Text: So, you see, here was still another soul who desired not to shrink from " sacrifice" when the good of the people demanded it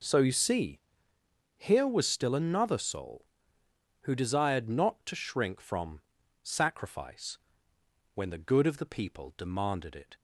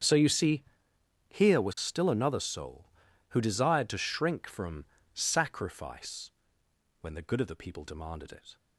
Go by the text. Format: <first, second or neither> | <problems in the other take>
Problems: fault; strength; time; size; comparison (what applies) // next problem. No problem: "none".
first | starts louder than the rest; strong; until 1.6 s; 8 dB // skips "not"; at 3.8 s // pauses between "sacrifice" and "when"; noticeable; at 6.2 s; 0.70 s long; noticeable in the first